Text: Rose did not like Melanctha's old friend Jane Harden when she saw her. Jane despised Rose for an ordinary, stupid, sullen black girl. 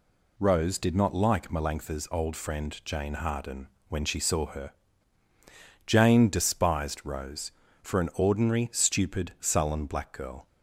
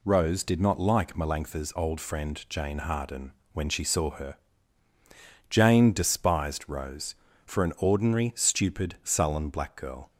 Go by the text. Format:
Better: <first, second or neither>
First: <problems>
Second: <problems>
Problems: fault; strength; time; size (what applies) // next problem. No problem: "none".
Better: neither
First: pauses between "Harden" and "when"; slight; at 3.6 s; 0.20 s long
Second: pauses between "Harden" and "when"; slight; at 3.3 s; 0.20 s long